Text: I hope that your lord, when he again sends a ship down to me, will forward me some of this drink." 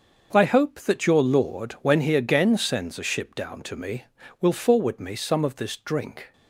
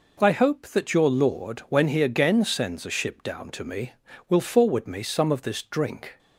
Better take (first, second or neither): second